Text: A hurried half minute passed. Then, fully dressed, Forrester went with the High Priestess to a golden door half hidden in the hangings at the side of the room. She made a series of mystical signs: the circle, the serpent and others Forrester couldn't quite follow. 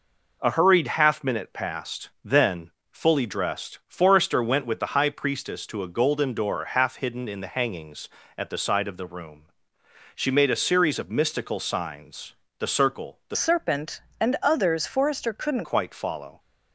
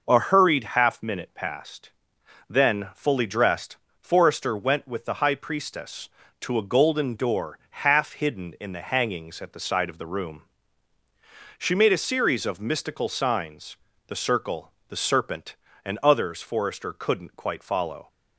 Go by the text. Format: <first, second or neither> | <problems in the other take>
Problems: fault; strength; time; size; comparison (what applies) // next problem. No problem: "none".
second | changes voice from "serpent" to "couldn't"; from 13.3 to 15.6 s; 2.3 s long